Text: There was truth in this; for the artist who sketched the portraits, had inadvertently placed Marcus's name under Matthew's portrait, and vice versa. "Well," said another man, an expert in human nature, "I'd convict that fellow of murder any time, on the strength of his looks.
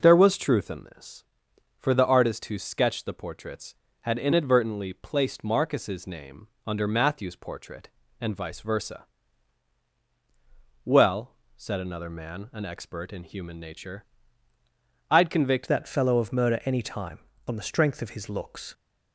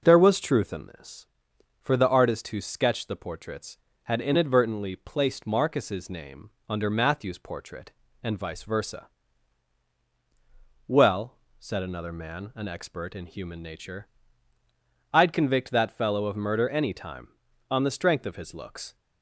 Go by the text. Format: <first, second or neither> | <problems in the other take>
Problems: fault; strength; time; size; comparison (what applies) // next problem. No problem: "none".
second | pauses between "name" and "under"; slight; at 6.4 s; 0.18 s long; slight in the second // changes voice at "that"; from 15.6 s on; 3.1 s long